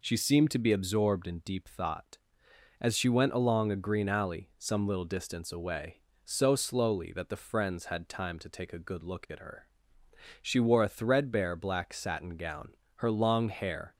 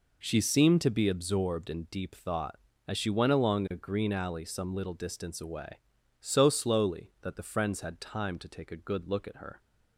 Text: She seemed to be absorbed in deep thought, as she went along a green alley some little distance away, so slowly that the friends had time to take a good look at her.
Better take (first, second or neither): second